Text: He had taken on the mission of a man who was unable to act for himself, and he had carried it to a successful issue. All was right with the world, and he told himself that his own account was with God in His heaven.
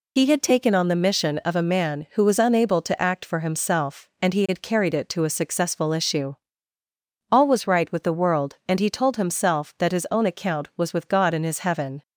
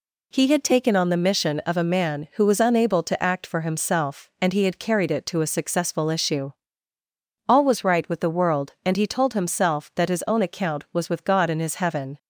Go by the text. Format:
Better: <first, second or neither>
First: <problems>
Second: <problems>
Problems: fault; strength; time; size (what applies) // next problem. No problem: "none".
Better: second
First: loses the start of "He"; at 0.1 s; 45 ms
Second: none